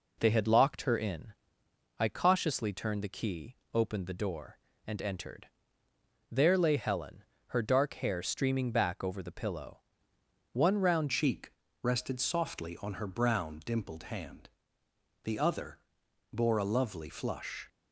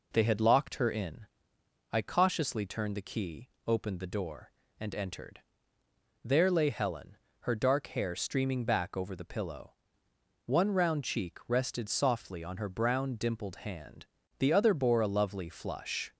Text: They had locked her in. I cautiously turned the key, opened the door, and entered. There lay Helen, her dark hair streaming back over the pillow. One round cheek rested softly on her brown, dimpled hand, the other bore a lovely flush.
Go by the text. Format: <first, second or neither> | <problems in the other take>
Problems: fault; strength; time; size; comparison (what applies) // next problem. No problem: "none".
second | changes voice at "cheek"; from 11.1 s on; 6.5 s long // pauses between "cheek" and "rested"; slight; at 11.5 s; 0.30 s long // pauses between "other" and "bore"; noticeable; at 15.7 s; 0.54 s long